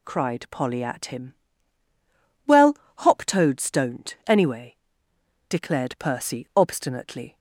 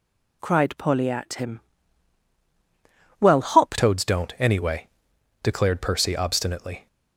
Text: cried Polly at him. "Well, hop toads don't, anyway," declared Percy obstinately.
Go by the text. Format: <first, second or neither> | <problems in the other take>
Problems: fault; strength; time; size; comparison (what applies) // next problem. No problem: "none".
first | changes voice at "toads"; from 3.7 s on; 3.1 s long